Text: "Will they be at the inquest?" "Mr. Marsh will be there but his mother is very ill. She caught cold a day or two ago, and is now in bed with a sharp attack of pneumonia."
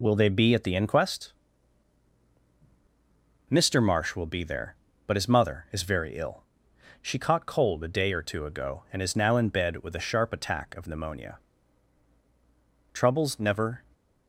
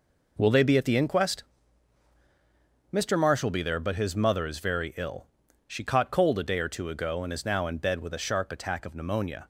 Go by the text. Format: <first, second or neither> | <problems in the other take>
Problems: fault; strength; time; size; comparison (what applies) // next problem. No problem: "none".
second | goes on to say "Troubles never"; noticeable; from 12.9 s on; 0.90 s long